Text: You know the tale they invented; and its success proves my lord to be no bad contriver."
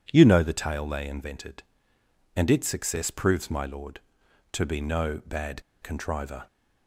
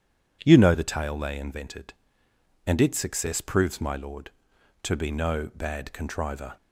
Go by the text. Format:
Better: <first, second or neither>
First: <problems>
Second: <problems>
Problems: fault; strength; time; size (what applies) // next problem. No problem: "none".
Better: second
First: pauses between "bad" and "contriver"; slight; at 5.6 s; 0.22 s long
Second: none